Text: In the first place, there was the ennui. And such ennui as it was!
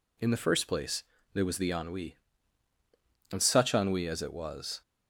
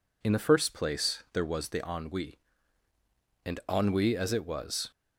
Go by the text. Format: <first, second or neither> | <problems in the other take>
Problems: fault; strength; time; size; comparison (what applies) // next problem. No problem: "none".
first | skips "such"; at 3.6 s